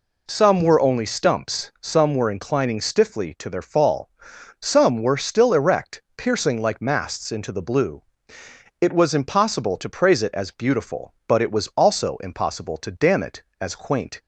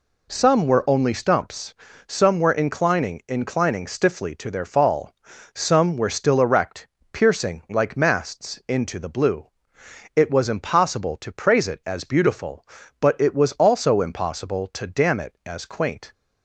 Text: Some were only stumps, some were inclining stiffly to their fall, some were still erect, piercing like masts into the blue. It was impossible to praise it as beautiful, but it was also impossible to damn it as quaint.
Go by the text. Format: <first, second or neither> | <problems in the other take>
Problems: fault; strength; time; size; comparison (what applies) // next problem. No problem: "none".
first | says "inclining" twice; at 3.2 s